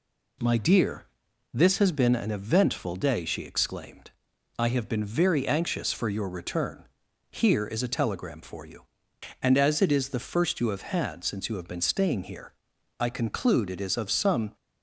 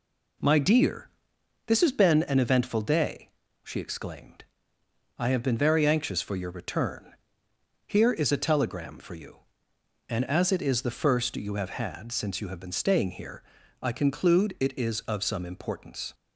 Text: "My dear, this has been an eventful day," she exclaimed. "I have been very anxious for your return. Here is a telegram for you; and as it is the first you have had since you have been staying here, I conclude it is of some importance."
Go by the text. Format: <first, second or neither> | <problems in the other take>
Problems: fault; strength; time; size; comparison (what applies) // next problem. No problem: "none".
second | stops before "importance"; at 14.5 s